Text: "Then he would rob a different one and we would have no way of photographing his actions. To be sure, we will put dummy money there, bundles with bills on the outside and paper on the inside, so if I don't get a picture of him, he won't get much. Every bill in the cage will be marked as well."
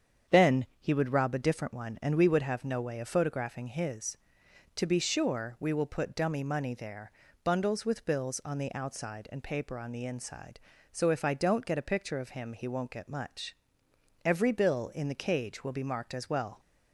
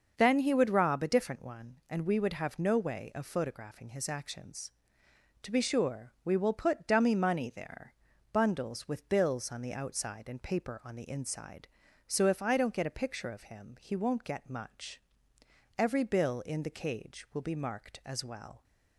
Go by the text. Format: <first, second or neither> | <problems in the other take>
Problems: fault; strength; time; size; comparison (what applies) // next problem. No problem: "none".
second | starts louder than the rest; strong; until 1.4 s; 8 dB; also in the second // pauses between "Then" and "he"; slight; at 0.6 s; 0.16 s long // skips "actions"; at 4.4 s